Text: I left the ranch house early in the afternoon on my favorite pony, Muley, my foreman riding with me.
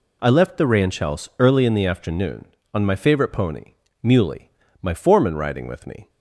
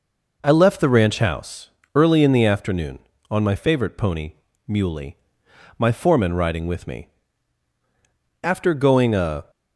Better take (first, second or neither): first